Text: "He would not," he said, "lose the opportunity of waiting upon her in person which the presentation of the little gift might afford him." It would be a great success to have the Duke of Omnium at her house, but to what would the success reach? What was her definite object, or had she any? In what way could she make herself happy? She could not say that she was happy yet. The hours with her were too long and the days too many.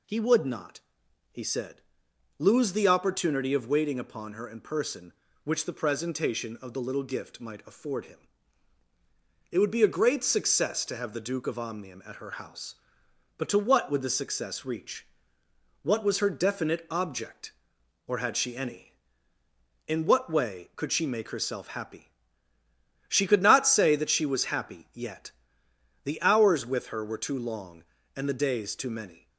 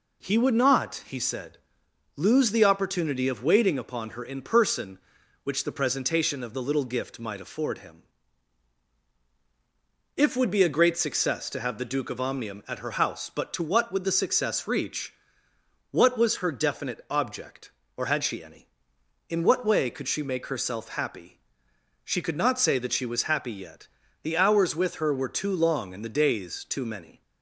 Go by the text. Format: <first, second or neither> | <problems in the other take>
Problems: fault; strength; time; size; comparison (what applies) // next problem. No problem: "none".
first | says "If" for "It"; at 10.1 s